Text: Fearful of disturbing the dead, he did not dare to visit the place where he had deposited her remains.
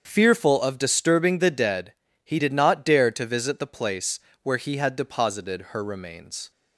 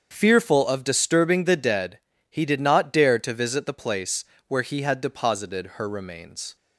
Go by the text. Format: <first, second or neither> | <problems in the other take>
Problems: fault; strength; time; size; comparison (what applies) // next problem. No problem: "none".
neither | starts louder than the rest; the same in both // pauses between "place" and "where"; slight; the same in both